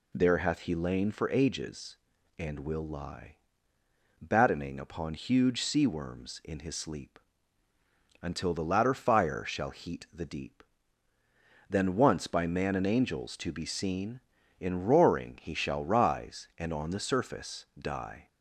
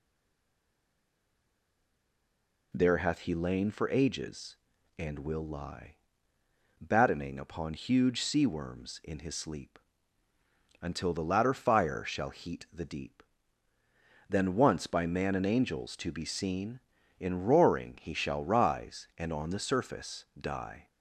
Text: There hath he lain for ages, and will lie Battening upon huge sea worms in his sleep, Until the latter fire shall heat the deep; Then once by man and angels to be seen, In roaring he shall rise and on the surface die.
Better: first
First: pauses between "lie" and "Battening"; noticeable; at 3.3 s; 0.84 s long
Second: stays silent before the first word; strong; until 2.7 s; 2.7 s long // pauses between "lie" and "Battening"; noticeable; at 5.9 s; 0.84 s long

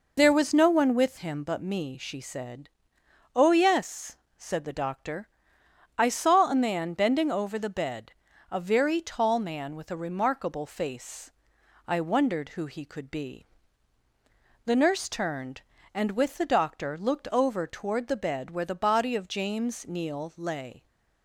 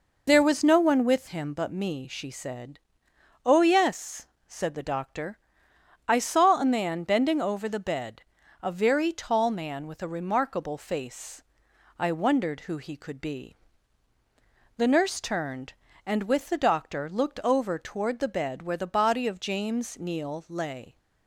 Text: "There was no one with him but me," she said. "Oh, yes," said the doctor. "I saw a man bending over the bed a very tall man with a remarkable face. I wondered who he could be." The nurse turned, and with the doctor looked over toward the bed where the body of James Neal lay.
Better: neither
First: pauses between "bed" and "a"; at 8.1 s; 0.38 s long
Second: pauses between "bed" and "a"; at 8.2 s; 0.40 s long

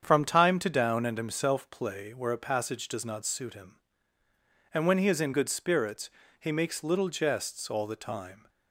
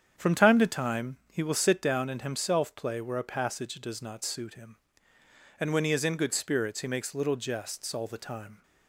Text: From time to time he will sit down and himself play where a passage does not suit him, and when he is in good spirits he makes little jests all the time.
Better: second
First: starts louder than the rest; strong; until 1.0 s; 8 dB // skips "time he will sit"; at 0.6 s // pauses between "spirits" and "he"; slight; at 6.1 s; 0.30 s long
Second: starts louder than the rest; strong; until 1.1 s; 8 dB

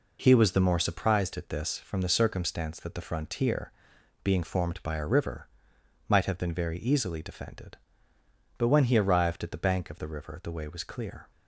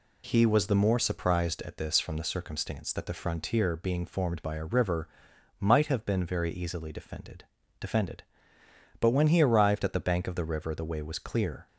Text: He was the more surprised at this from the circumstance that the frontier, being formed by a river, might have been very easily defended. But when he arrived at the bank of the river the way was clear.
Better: first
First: none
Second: says "defended" twice; at 7.7 s

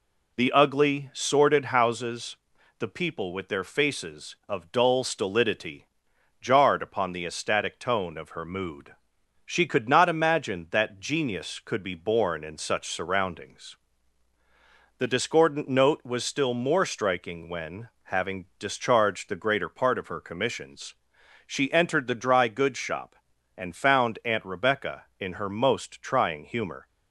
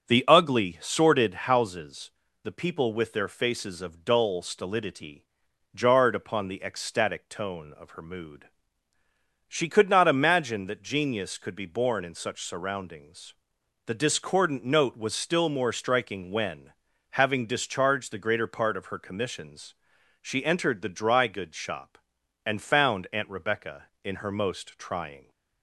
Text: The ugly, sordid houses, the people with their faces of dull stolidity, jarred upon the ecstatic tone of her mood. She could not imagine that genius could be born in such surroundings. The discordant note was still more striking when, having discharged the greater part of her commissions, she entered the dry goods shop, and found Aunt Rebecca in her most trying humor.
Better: first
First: none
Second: starts louder than the rest; strong; until 1.1 s; 7 dB // stops before "humor"; at 25.2 s

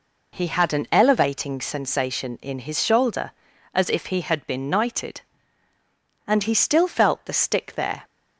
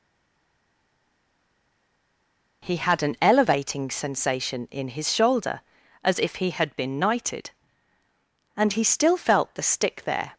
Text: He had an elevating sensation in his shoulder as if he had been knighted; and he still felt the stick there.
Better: first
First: none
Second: stays silent before the first word; strong; until 2.6 s; 2.6 s long

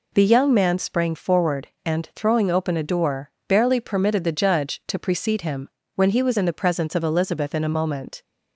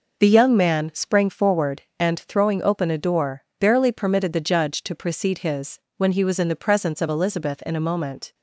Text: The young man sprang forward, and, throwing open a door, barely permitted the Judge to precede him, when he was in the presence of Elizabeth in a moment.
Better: first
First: none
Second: says "his" for "him"; at 5.3 s

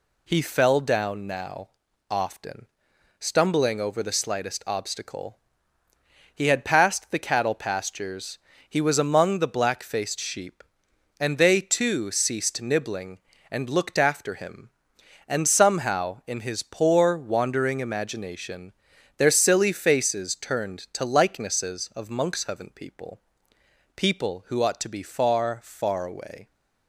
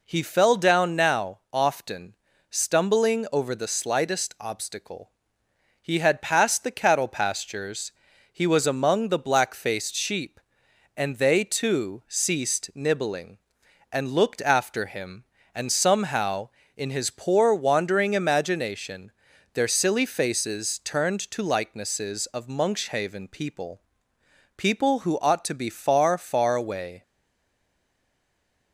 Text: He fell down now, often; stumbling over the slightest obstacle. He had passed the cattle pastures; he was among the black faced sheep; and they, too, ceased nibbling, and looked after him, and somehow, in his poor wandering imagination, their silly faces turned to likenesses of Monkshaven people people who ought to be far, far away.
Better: first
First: pauses between "people" and "people"; noticeable; at 23.2 s; 0.74 s long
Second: pauses between "people" and "people"; noticeable; at 23.7 s; 0.78 s long // stays silent after the last word; noticeable; from 27.0 s on; 1.7 s long

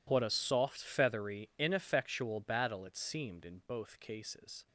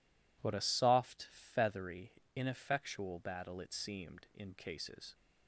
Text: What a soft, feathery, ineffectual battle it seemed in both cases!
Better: first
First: none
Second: skips "both"; at 4.5 s

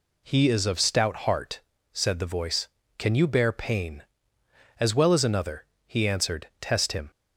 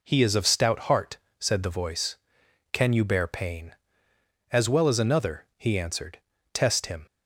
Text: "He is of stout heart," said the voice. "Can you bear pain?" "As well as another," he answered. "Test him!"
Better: neither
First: none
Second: none

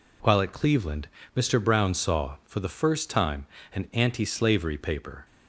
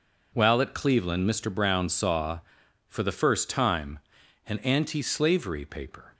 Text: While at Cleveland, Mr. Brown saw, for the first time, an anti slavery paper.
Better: neither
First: none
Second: none

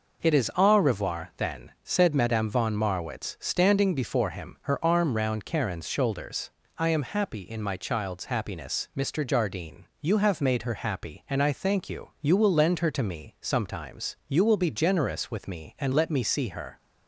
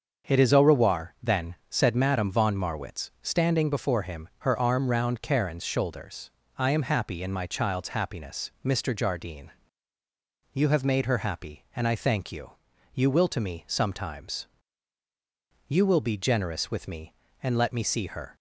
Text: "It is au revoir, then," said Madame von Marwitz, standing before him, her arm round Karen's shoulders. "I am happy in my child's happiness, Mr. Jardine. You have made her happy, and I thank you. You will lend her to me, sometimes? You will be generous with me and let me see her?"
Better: first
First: none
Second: starts louder than the rest; until 1.3 s; 6.5 dB // skips "lend her"; at 13.2 s

